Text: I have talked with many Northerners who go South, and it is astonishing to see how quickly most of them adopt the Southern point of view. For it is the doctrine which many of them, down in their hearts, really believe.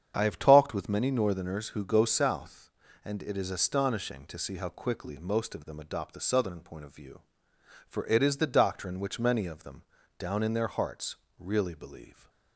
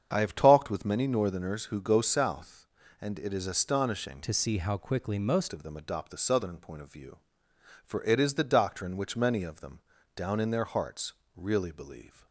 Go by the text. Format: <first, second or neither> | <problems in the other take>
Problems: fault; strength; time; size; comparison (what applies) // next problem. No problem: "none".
first | starts louder than the rest; strong; until 1.1 s; 7.5 dB; strong in the first // changes voice from "to" to "most"; from 4.2 to 5.5 s; 1.3 s long